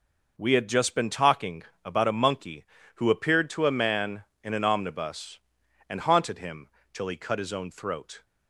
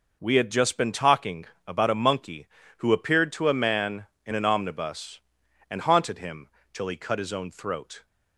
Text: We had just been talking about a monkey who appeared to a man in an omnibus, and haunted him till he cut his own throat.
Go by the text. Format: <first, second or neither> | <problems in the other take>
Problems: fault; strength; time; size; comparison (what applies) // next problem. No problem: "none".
neither | pauses between "talking" and "about"; slight; the same in both // pauses between "him" and "till"; slight; the same in both